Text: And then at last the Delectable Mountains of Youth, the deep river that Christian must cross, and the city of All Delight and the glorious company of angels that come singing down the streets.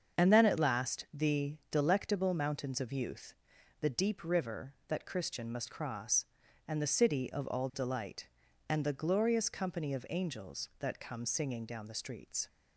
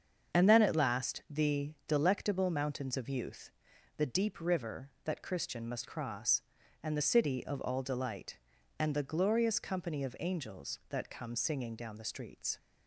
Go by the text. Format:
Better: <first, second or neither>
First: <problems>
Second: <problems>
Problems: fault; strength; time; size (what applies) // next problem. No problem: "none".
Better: neither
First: starts louder than the rest; until 1.2 s; 7 dB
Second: starts louder than the rest; until 1.4 s; 7 dB